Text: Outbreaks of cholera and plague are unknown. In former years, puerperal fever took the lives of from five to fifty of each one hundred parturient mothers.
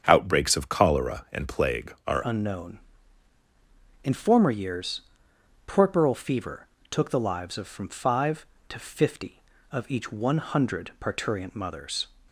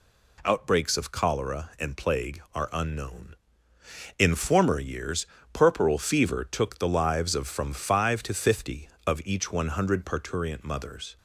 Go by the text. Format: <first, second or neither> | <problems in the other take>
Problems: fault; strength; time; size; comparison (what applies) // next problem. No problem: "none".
second | starts louder than the rest; strong; until 1.0 s; 7.5 dB // changes voice at "unknown"; from 2.2 s on; 9.8 s long // pauses between "fever" and "took"; slight; at 6.6 s; 0.24 s long